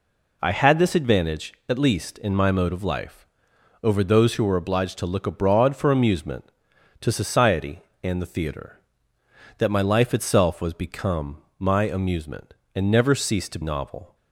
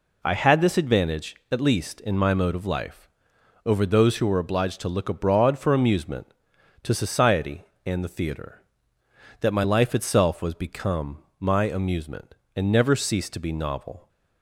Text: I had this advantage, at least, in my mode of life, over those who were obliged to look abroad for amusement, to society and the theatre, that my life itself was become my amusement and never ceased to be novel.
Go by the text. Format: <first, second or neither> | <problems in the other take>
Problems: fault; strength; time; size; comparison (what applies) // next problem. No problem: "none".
second | pauses between "become" and "my"; slight; at 11.4 s; 0.16 s long; slight in the second // skips "be"; at 13.6 s